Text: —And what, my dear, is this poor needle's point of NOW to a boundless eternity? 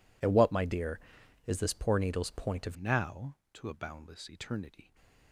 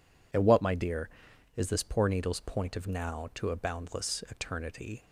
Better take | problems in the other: second | changes voice at "NOW"; from 2.7 s on; 2.2 s long

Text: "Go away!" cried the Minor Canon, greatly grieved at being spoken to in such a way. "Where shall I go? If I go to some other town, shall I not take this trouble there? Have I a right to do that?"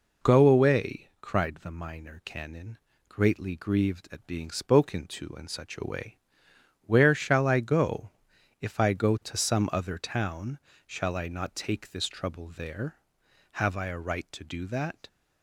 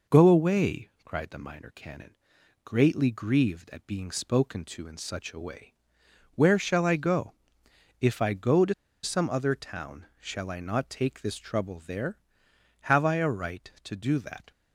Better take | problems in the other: first | pauses between "to" and "some"; slight; at 8.7 s; 0.29 s long

